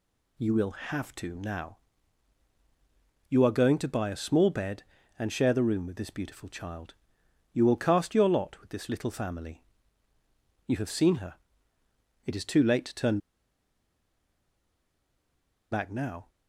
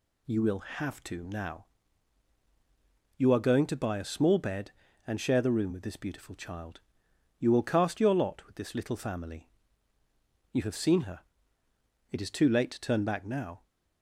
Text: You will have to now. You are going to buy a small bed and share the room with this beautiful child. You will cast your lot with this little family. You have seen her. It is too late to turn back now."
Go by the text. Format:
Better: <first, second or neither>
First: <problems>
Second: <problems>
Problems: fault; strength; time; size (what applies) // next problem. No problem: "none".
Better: second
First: pauses between "turn" and "back"; strong; at 13.1 s; 2.5 s long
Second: none